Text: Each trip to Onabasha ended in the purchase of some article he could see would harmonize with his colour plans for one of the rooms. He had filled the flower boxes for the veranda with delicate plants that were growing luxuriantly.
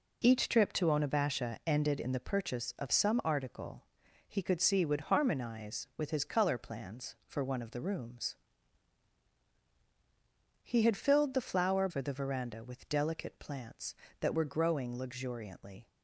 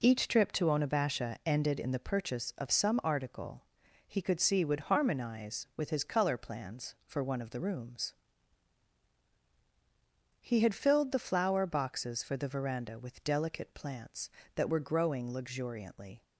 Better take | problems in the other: second | pauses between "article" and "he"; noticeable; at 3.8 s; 0.46 s long; noticeable in the second // skips "boxes"; at 11.8 s

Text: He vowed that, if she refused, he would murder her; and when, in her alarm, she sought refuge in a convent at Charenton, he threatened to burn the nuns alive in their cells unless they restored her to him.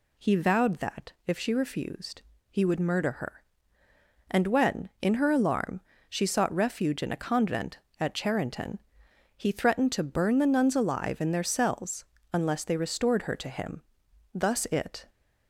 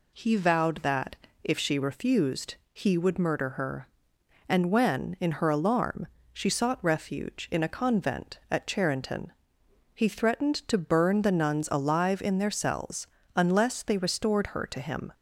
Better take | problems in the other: second | pauses between "cells" and "unless"; slight; at 12.0 s; 0.28 s long; slight in the second // goes on to say "Thus it"; noticeable; from 14.3 s on; 0.74 s long

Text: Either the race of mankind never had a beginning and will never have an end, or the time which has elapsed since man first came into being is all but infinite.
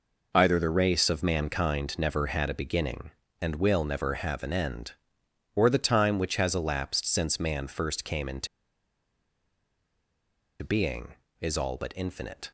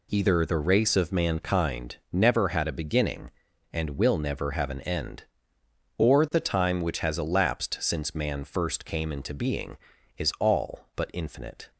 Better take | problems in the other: second | pauses between "into" and "being"; strong; at 8.4 s; 2.1 s long

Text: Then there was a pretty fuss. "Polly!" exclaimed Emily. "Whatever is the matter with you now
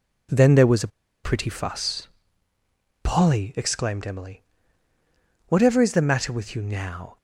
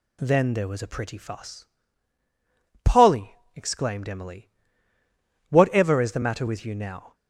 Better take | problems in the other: second | pauses between "a" and "pretty"; slight; at 0.8 s; 0.35 s long

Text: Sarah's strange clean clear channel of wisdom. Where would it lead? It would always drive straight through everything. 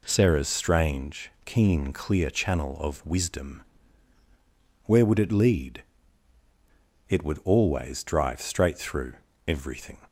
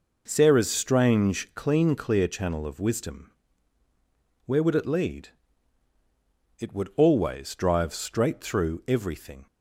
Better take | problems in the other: second | says "keen" for "clean"; at 1.4 s // pauses between "through" and "everything"; slight; at 9.1 s; 0.34 s long

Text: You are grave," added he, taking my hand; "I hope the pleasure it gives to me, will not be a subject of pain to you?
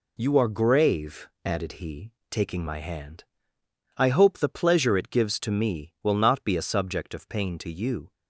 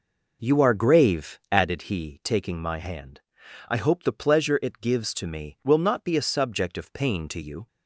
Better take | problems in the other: first | starts louder than the rest; noticeable; until 1.8 s; 5 dB

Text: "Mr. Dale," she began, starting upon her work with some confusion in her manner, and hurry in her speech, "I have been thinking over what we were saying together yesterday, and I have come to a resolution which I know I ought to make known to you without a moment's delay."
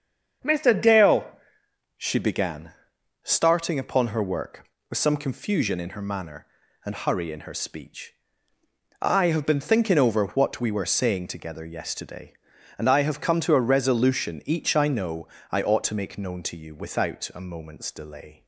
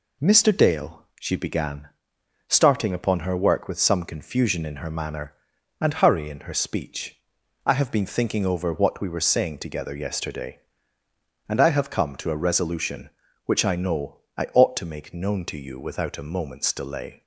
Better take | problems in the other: second | starts louder than the rest; until 2.0 s; 7 dB // says "each" for "which"; at 14.4 s // pauses between "know" and "I"; slight; at 15.2 s; 0.24 s long; slight in the second

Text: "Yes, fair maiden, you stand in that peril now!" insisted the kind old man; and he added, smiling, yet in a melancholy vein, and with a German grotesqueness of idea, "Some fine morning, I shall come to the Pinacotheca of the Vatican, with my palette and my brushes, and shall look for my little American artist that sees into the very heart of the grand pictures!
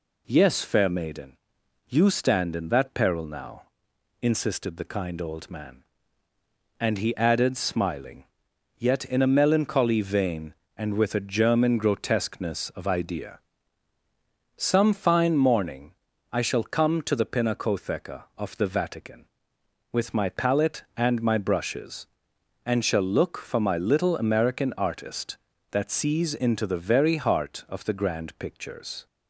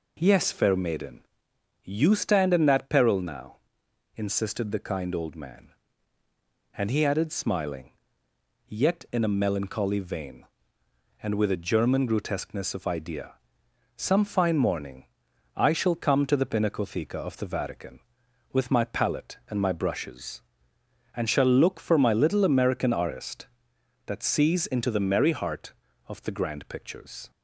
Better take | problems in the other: first | says "merry" for "very"; at 25.0 s

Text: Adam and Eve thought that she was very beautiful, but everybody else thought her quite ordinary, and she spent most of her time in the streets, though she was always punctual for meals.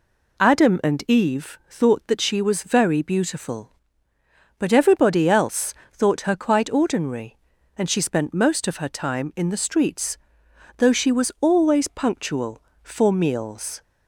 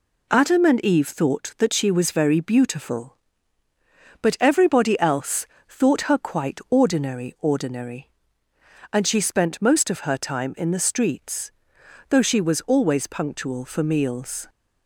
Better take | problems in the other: first | pauses between "else" and "thought"; slight; at 5.4 s; 0.22 s long; slight in the first // says "ordinary" twice; at 7.3 s

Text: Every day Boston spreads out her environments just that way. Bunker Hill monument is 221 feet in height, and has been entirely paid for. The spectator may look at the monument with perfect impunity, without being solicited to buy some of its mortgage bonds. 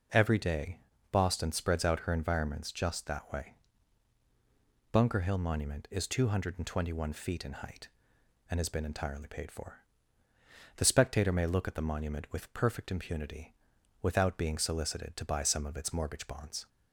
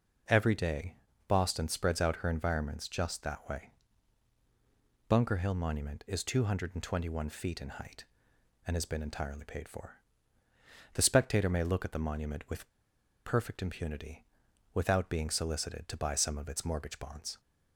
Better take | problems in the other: first | pauses between "day" and "Boston"; slight; at 0.9 s; 0.32 s long; slight in the first // pauses between "with" and "perfect"; noticeable; at 12.6 s; 0.57 s long

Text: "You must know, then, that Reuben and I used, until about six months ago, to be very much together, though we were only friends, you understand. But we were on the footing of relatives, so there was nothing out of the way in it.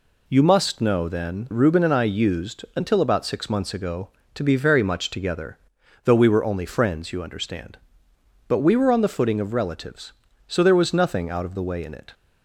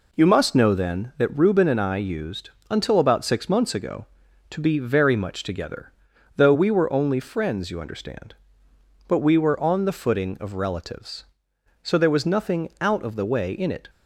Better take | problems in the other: second | skips "that"; at 1.5 s

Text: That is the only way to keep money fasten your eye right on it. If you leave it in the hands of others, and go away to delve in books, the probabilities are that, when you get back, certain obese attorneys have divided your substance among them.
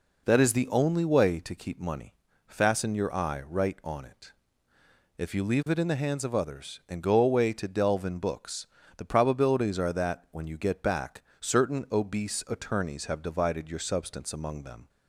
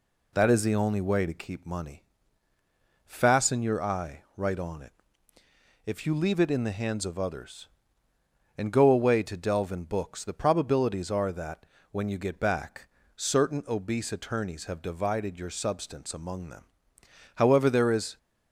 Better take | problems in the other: first | pauses between "money" and "fasten"; at 2.0 s; 1.0 s long; slight in the first // goes on to say "However there is"; noticeable; from 17.3 s on; 0.82 s long

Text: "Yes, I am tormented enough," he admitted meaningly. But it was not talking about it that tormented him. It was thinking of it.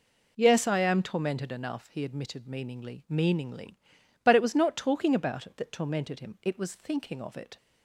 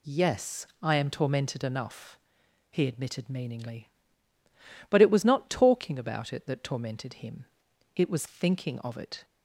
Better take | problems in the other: second | says "meaningly" twice; at 3.0 s

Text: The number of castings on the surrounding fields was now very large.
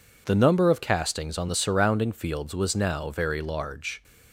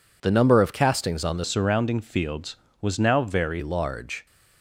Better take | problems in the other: first | changes voice from "surrounding" to "very"; from 1.4 to 3.6 s; 2.2 s long

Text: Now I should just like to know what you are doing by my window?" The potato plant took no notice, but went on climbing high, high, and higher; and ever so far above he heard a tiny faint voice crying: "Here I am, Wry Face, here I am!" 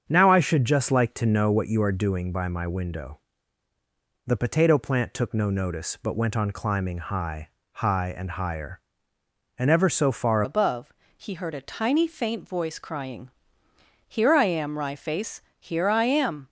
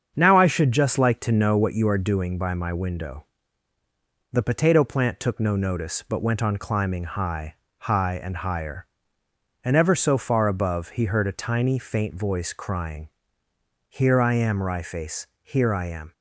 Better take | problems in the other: second | starts louder than the rest; strong; until 1.0 s; 7.5 dB; strong in the second // changes voice at "above"; from 10.4 s on; 6.0 s long // pauses between "above" and "he"; slight; at 10.9 s; 0.24 s long

